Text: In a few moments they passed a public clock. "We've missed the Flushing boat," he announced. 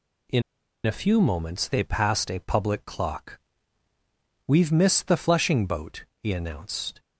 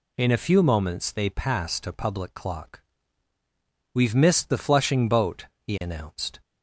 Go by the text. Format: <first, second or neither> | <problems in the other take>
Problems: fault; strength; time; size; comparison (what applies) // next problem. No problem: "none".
second | pauses between "In" and "a"; at 0.4 s; 0.43 s long